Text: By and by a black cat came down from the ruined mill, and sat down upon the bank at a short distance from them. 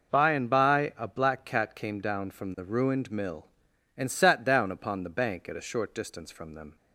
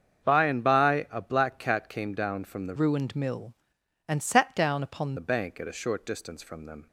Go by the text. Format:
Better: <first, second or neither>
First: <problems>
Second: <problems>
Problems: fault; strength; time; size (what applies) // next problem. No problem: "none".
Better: first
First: none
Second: starts louder than the rest; until 1.2 s; 7 dB // changes voice from "ruined" to "upon"; from 2.7 to 5.1 s; 2.4 s long